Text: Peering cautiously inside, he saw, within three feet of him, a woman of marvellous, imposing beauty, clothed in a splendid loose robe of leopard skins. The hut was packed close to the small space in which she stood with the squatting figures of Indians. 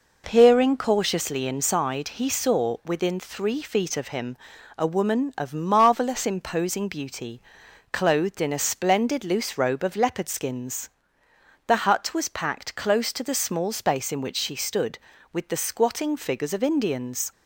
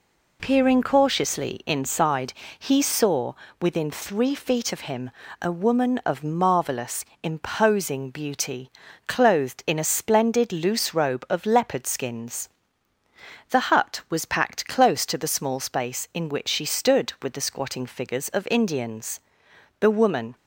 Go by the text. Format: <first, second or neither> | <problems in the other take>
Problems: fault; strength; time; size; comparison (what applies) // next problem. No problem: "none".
first | goes on to say "The woman"; from 19.7 s on; 0.56 s long